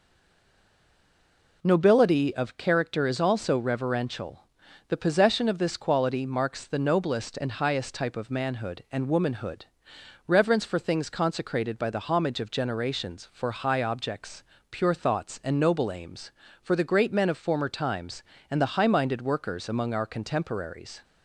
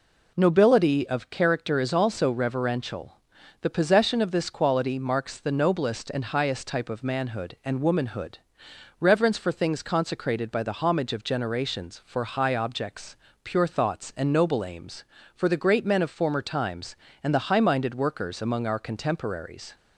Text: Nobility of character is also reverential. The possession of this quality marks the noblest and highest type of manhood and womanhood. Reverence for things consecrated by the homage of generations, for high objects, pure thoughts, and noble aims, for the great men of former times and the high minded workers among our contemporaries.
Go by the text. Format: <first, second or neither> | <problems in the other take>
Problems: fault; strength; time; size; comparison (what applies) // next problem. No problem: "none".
second | stays silent before the first word; noticeable; until 1.6 s; 1.6 s long